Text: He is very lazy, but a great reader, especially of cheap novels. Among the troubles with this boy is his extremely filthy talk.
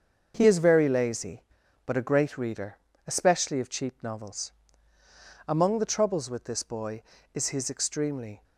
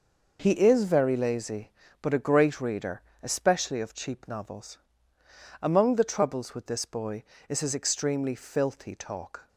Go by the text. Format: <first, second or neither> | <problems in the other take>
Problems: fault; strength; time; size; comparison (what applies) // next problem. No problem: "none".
second | starts louder than the rest; until 1.3 s; 6.5 dB // stops before "filthy talk"; at 8.4 s